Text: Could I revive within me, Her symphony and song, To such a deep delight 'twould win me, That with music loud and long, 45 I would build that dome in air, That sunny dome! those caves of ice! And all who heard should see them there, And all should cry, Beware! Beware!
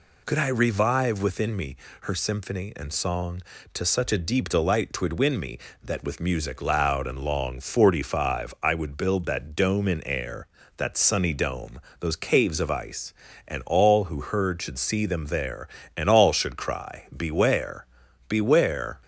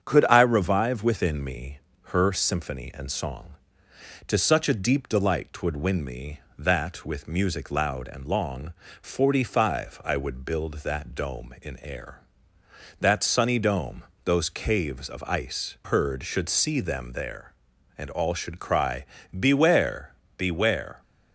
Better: first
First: none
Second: starts louder than the rest; strong; until 1.0 s; 8 dB // skips "And all who"; at 15.7 s

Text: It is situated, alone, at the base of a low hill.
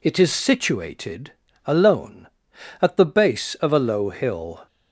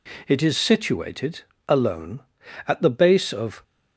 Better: first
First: none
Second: stops before "a low hill"; at 3.6 s

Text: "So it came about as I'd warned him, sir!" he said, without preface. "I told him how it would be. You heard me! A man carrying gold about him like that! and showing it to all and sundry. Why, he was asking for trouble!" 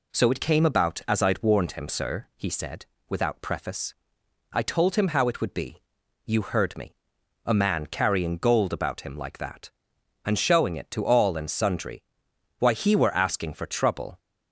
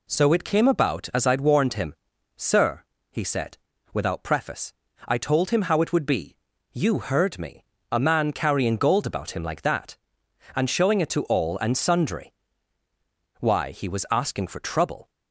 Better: second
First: says "were" for "was"; at 12.9 s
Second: none

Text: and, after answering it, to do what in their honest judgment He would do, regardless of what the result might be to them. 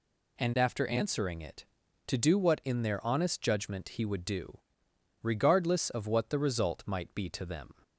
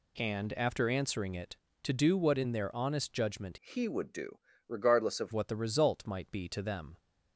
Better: first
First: none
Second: changes voice from "He" to "of"; from 3.5 to 5.3 s; 1.8 s long

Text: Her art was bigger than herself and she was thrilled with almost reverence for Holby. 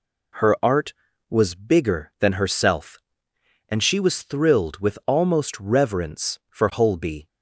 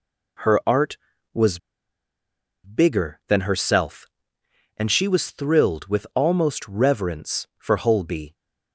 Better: first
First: none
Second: pauses between "was" and "bigger"; at 1.5 s; 1.0 s long

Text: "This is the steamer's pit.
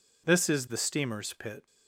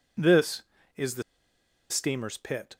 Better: first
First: none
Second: pauses between "the" and "steamer's"; noticeable; at 1.2 s; 0.68 s long

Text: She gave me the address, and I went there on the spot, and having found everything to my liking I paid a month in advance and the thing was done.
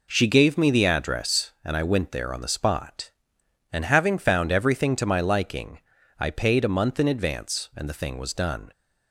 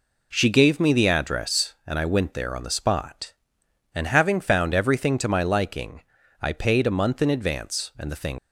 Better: first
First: pauses between "liking" and "I"; at 5.7 s; 0.40 s long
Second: pauses between "liking" and "I"; at 5.9 s; 0.40 s long // stops before "was done"; at 8.3 s

